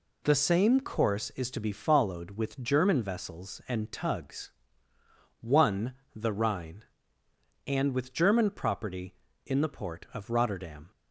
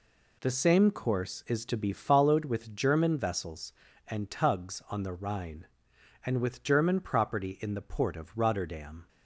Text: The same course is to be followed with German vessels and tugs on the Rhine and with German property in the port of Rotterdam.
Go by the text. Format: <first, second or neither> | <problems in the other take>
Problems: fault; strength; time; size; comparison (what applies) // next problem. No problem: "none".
second | says "one" for "on"; at 5.4 s